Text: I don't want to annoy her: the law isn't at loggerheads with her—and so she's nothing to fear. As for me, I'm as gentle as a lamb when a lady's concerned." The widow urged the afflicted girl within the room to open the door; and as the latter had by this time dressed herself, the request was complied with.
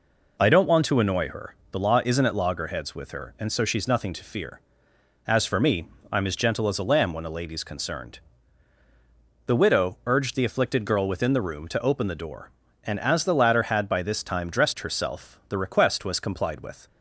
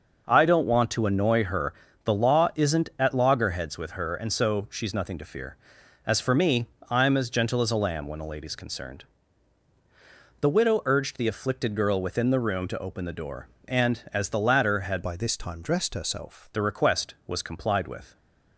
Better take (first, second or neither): first